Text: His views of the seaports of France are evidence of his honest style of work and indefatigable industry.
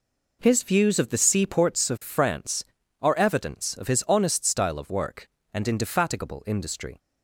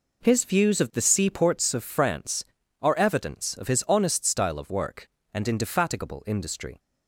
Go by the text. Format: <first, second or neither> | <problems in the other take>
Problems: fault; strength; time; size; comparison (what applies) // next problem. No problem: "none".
neither | none